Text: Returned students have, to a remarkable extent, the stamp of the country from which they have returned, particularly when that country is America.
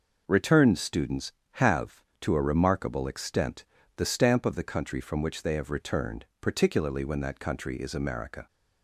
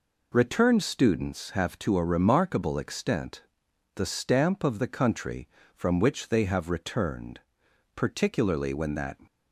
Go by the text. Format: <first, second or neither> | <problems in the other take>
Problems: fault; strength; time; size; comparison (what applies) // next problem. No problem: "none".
first | stops before "country is America"; at 9.2 s